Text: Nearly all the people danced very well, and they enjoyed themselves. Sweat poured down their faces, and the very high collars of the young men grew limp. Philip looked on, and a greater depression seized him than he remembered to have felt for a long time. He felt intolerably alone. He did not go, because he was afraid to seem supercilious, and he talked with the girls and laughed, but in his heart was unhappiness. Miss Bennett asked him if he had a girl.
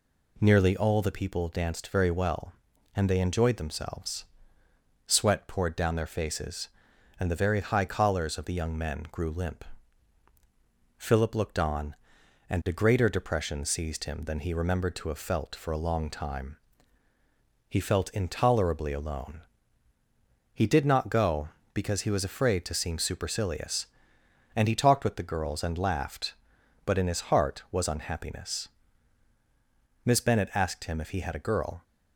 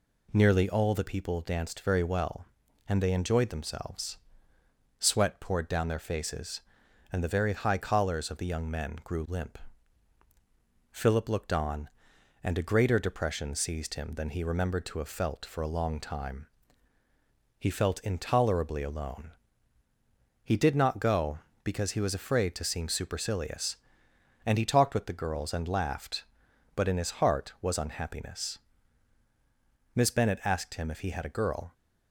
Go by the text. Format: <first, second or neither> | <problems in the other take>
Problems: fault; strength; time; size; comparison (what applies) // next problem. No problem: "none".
neither | none